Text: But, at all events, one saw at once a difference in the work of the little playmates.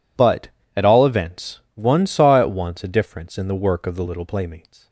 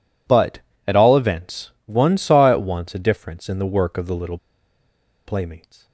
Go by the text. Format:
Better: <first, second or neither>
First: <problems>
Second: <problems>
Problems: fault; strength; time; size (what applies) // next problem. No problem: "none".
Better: first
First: none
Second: pauses between "little" and "playmates"; noticeable; at 4.3 s; 0.87 s long